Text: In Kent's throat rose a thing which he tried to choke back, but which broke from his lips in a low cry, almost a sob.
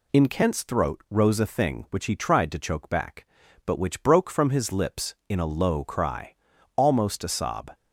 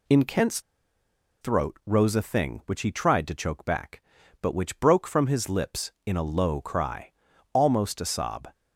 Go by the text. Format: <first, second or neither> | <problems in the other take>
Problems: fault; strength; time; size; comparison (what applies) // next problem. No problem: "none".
first | pauses between "Kent's" and "throat"; noticeable; at 0.5 s; 0.81 s long